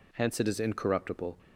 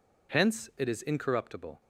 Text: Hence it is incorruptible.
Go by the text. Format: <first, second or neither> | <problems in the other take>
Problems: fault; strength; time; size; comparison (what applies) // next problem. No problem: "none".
neither | none